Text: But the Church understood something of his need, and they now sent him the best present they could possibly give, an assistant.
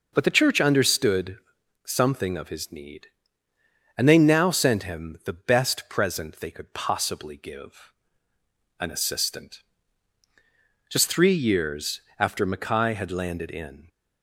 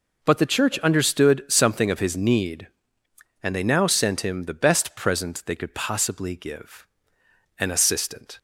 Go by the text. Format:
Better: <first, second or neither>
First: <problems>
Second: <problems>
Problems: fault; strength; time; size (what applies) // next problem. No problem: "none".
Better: second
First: pauses between "understood" and "something"; noticeable; at 1.3 s; 0.46 s long // goes on to say "Just three years after Mackay had landed in"; strong; from 10.8 s on; 3.0 s long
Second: none